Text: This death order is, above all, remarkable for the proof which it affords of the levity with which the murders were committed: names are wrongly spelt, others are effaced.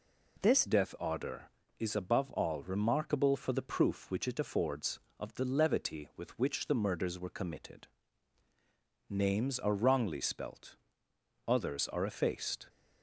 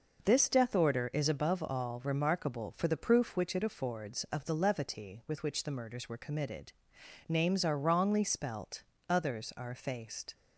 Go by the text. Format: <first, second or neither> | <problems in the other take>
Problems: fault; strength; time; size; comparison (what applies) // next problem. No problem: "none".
second | changes voice at "death"; from 0.6 s on; 12.0 s long